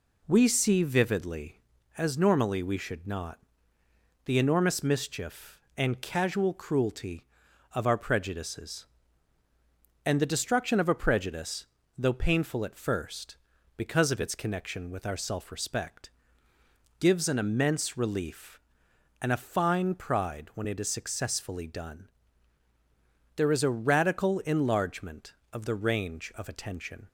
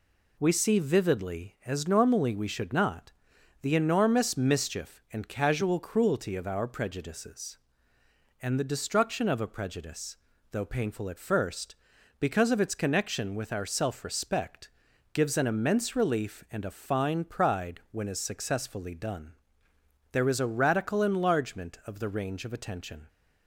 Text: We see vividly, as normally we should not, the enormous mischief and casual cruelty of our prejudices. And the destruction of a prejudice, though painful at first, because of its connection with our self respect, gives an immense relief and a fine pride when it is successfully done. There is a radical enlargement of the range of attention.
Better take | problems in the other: first | skips "it"; at 18.0 s

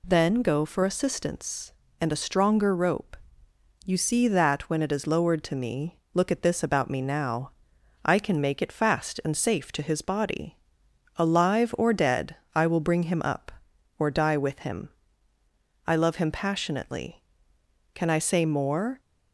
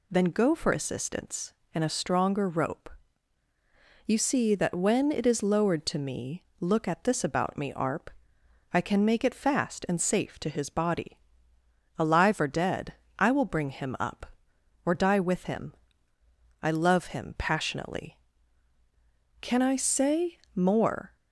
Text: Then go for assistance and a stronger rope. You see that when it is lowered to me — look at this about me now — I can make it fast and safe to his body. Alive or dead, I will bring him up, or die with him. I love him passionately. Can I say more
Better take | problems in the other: first | says "arp" for "now"; at 7.7 s // pauses between "say" and "more"; slight; at 20.3 s; 0.16 s long

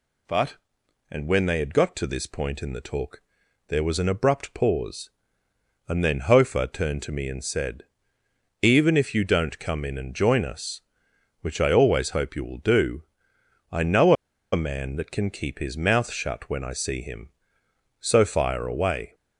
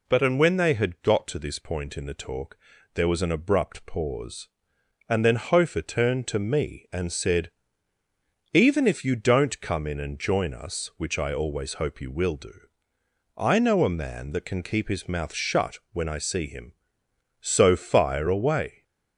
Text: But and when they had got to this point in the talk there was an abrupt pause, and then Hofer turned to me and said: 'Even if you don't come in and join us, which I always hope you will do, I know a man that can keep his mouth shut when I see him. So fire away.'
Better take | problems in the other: second | pauses between "talk" and "there"; noticeable; at 3.2 s; 0.46 s long; slight in the second // pauses between "know" and "a"; at 14.1 s; 0.39 s long

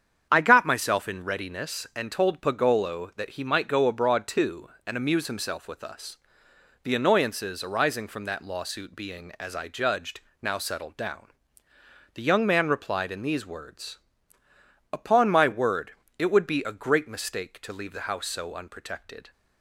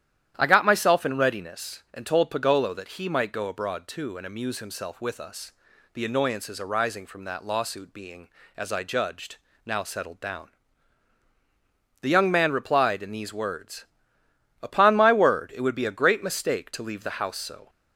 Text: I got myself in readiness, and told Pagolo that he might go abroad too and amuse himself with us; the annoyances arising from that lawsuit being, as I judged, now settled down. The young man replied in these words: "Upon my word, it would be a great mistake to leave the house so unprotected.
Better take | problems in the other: first | starts louder than the rest; strong; until 1.3 s; 11 dB; strong in the first // stops before "unprotected"; at 17.6 s

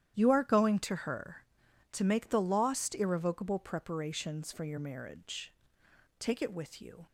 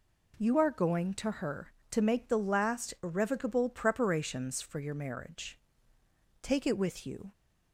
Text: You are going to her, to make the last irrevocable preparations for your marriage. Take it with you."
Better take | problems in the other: second | starts louder than the rest; strong; until 1.2 s; 11 dB // says "lost" for "last"; at 2.4 s

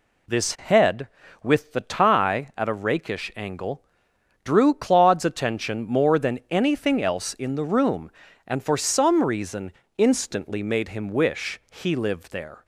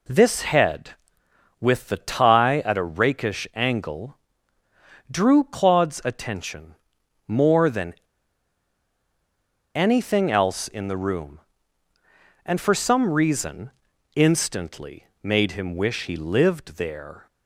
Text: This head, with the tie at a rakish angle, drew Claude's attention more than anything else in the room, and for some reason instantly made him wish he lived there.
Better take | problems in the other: first | pauses between "attention" and "more"; noticeable; at 6.7 s; 0.50 s long // pauses between "than" and "anything"; strong; at 7.9 s; 1.8 s long // pauses between "reason" and "instantly"; at 13.7 s; 0.44 s long; slight in the first

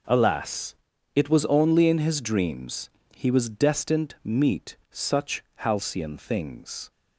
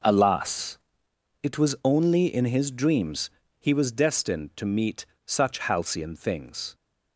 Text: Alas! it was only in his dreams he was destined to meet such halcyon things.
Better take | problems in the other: second | pauses between "dreams" and "he"; slight; at 2.8 s; 0.26 s long; slight in the second // skips "to"; at 4.1 s // pauses between "meet" and "such"; slight; at 4.7 s; 0.16 s long; slight in the second

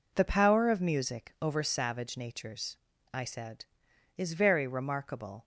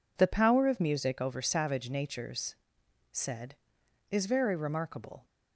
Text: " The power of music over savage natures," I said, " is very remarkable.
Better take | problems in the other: first | skips "I"; at 2.8 s

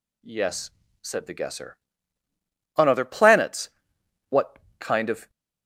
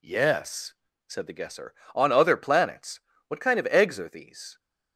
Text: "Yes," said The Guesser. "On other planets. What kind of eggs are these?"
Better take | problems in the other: second | pauses between "What" and "kind"; slight; at 4.5 s; 0.20 s long // stops before "eggs are these"; at 5.2 s

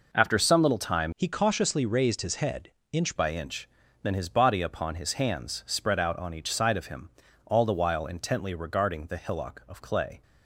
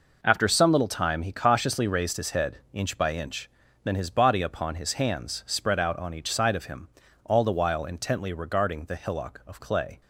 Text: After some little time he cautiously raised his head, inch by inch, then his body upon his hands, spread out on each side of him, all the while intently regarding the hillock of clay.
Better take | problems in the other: second | changes voice from "he" to "inch"; from 1.1 to 3.1 s; 2.0 s long

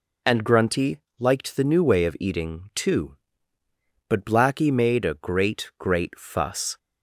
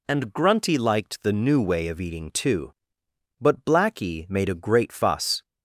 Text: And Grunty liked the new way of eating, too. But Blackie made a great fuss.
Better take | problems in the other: second | pauses between "Grunty" and "liked"; slight; at 0.9 s; 0.22 s long // says "great" twice; at 5.7 s

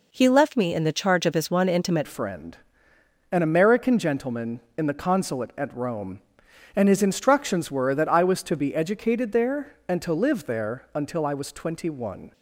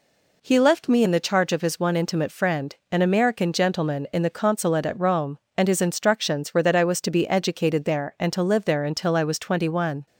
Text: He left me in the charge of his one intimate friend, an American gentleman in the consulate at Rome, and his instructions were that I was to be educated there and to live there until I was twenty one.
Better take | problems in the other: second | changes voice at "friend"; from 2.0 s on; 10.3 s long

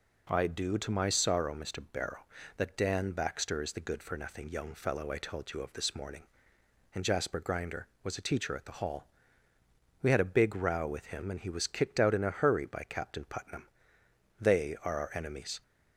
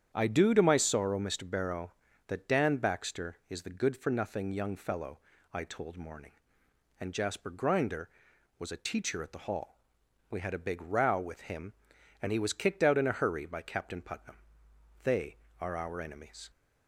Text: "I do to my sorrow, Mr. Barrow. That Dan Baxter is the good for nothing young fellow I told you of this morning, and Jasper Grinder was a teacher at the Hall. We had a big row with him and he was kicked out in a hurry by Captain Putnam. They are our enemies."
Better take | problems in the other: first | starts louder than the rest; strong; until 1.1 s; 8.5 dB // pauses between "fellow" and "I"; slight; at 5.1 s; 0.34 s long // skips "you of this"; at 5.9 s

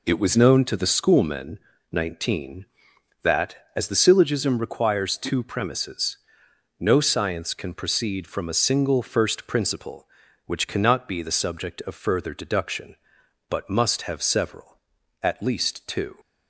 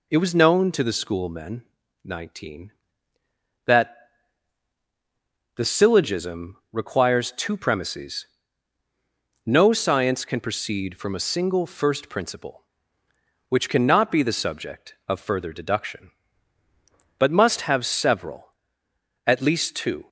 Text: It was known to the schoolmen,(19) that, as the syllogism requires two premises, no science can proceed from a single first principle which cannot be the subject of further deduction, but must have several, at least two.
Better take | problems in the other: first | skips "as"; at 4.8 s // pauses between "syllogism" and "requires"; slight; at 6.5 s; 0.16 s long

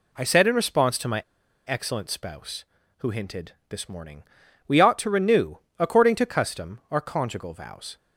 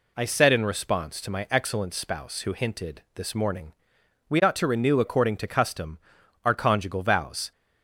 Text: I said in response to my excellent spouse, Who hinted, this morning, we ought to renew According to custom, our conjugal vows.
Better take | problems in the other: second | pauses between "my" and "excellent"; at 1.2 s; 0.44 s long // pauses between "renew" and "According"; slight; at 5.5 s; 0.20 s long

